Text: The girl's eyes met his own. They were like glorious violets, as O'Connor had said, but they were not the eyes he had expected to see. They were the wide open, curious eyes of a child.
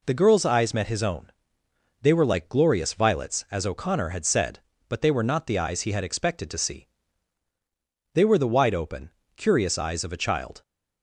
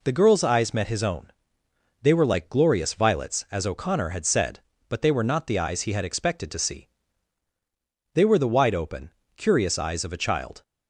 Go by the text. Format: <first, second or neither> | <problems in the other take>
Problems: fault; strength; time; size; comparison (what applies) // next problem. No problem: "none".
neither | none